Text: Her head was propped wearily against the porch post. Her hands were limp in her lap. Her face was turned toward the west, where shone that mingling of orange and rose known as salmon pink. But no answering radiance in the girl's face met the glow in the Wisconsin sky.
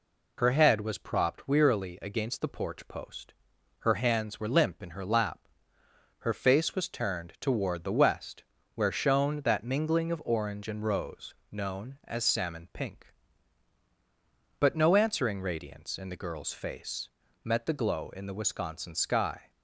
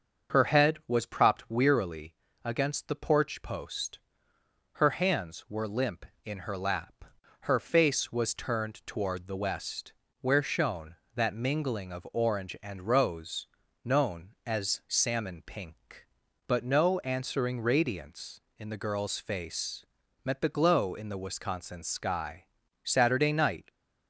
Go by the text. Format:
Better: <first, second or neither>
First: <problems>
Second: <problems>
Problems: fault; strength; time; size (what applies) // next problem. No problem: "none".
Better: first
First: pauses between "rose" and "known"; slight; at 11.3 s; 0.18 s long // pauses between "face" and "met"; slight; at 17.1 s; 0.34 s long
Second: starts louder than the rest; until 1.4 s; 6.5 dB // pauses between "wearily" and "against"; slight; at 2.1 s; 0.30 s long // pauses between "rose" and "known"; slight; at 13.4 s; 0.36 s long // pauses between "face" and "met"; at 19.8 s; 0.40 s long // goes on to say "Saturday night"; noticeable; from 22.8 s on; 0.86 s long